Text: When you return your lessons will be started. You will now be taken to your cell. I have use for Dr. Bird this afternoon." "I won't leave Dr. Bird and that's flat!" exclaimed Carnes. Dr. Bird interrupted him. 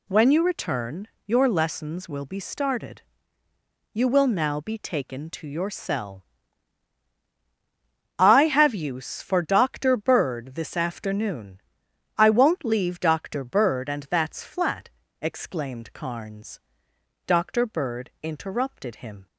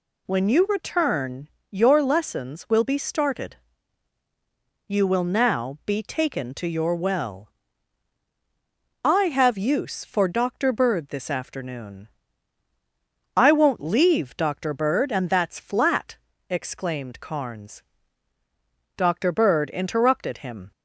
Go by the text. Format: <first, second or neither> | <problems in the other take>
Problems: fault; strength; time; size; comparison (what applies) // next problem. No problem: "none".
first | pauses between "return" and "your"; slight; at 1.4 s; 0.24 s long; slight in the first // says "well" for "cell"; at 6.9 s